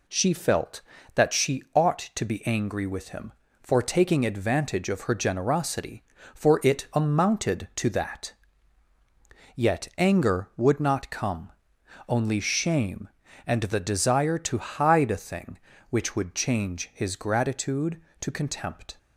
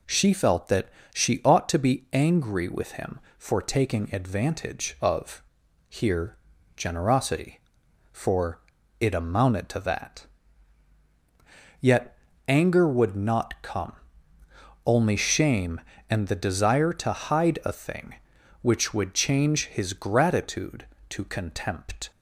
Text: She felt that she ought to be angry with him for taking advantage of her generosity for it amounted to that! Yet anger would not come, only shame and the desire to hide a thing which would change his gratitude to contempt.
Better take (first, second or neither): first